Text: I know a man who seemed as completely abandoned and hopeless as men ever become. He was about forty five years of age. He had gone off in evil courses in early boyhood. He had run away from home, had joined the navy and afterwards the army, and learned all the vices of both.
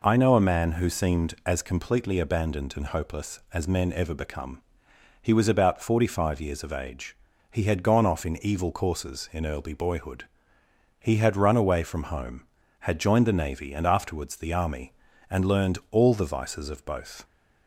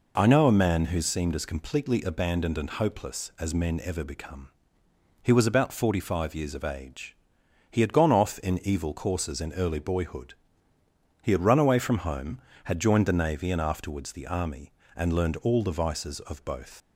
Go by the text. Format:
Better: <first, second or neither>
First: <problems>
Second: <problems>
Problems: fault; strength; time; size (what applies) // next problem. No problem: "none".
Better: first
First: none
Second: leaves "both" unfinished; at 16.8 s; 80 ms